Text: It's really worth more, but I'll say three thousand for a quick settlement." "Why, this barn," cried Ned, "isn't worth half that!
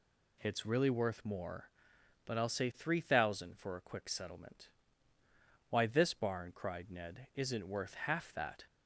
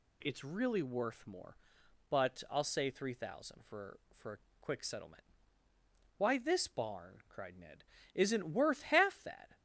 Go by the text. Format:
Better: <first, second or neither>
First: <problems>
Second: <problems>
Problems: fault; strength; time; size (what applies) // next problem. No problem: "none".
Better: first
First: none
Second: says "for" twice; at 4.1 s // pauses between "a" and "quick"; slight; at 4.3 s; 0.22 s long